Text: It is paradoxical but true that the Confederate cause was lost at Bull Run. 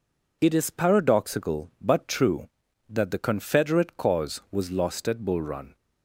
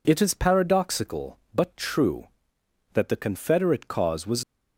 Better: first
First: none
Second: stops before "lost at Bull Run"; at 4.4 s

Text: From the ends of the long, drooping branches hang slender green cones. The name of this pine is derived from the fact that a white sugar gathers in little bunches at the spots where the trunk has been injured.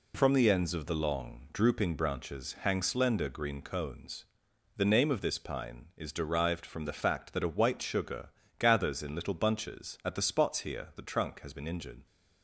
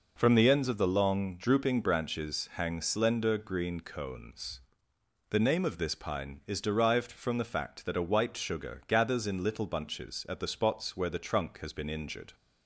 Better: second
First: pauses between "sugar" and "gathers"; slight; at 8.2 s; 0.28 s long // says "here" for "where"; at 10.5 s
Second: none

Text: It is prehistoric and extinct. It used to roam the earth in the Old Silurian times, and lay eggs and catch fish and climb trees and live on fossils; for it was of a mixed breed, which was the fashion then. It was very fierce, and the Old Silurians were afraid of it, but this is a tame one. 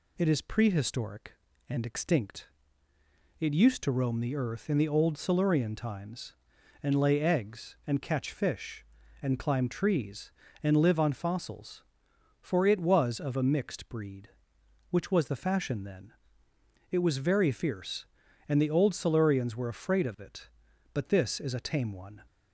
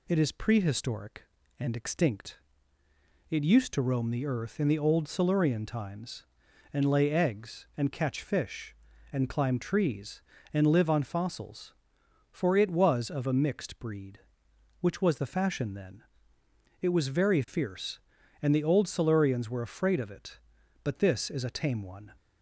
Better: neither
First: none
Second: none

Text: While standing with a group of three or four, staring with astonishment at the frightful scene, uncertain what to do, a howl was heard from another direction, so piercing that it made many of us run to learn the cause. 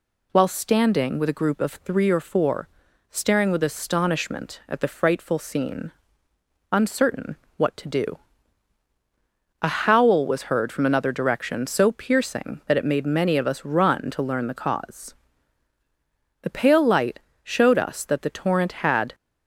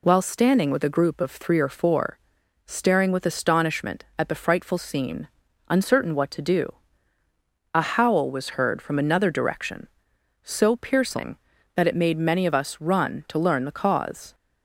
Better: second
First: pauses between "uncertain" and "what"; slight; at 7.3 s; 0.20 s long // goes on to say "The pale light showed us that the torrent had"; strong; from 16.4 s on; 2.7 s long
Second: none

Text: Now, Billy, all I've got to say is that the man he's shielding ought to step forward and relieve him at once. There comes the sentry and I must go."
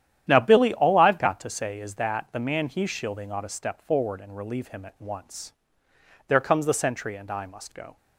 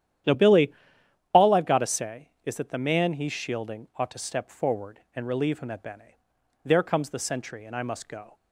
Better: first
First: starts louder than the rest; strong; until 1.2 s; 10.5 dB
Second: starts louder than the rest; strong; until 1.8 s; 11 dB // says "bene" for "once"; at 5.8 s

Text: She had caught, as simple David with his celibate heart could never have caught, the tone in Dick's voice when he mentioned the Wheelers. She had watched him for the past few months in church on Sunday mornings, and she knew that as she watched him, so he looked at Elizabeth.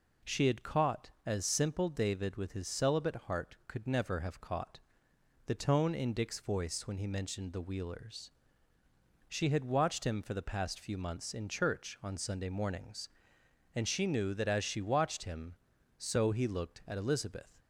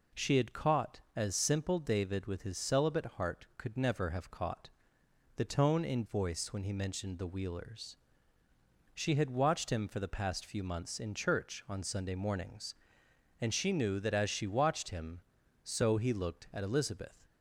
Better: first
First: none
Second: skips "Dick's"; at 6.0 s

